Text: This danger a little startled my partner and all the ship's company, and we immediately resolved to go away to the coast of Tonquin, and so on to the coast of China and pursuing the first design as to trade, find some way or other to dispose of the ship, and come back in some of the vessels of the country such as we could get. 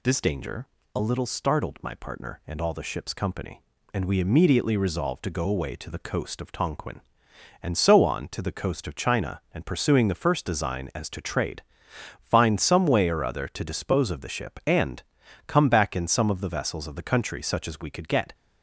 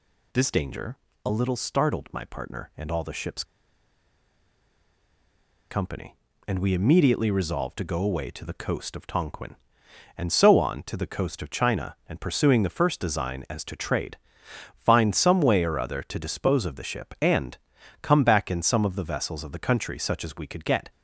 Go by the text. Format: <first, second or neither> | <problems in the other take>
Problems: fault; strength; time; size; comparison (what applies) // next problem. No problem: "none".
first | pauses between "danger" and "a"; slight; at 0.9 s; 0.28 s long; slight in the first // pauses between "ship's" and "company"; strong; at 3.4 s; 2.2 s long // pauses between "and" and "come"; at 17.5 s; 0.44 s long; also in the first